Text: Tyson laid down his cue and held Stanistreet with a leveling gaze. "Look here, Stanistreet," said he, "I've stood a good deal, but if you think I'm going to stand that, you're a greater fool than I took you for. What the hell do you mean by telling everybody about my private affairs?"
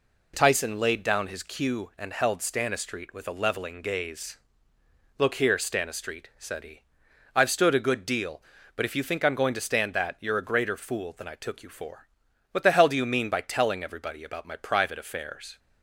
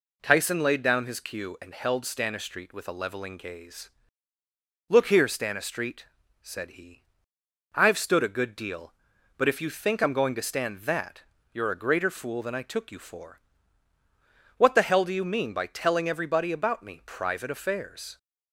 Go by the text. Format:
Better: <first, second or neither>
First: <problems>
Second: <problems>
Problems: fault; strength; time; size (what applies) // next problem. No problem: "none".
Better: first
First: none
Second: says "me" for "my"; at 16.8 s